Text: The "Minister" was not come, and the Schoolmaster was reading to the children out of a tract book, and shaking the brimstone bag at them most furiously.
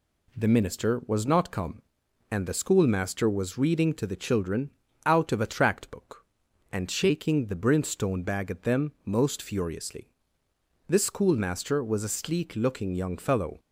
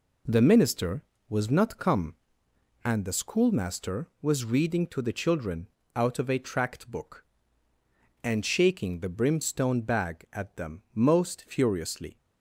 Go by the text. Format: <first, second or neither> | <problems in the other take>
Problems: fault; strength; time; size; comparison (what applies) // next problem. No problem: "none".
second | pauses between "children" and "out"; slight; at 4.6 s; 0.36 s long; slight in the second // goes on to say "This schoolmaster was a sleek looking young fellow"; strong; from 10.8 s on; 2.7 s long